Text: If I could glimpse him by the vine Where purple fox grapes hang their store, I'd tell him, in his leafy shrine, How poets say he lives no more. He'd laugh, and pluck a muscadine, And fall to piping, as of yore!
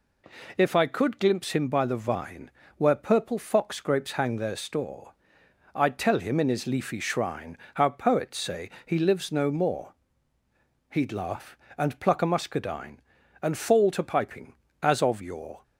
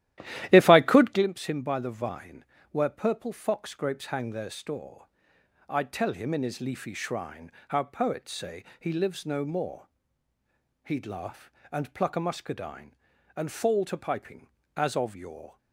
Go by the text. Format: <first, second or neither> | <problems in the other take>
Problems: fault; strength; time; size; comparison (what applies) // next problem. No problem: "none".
first | starts louder than the rest; strong; until 1.3 s; 13 dB // pauses between "vine" and "Where"; slight; at 2.4 s; 0.26 s long; slight in the first // pauses between "say" and "he"; slight; at 8.6 s; 0.16 s long; slight in the first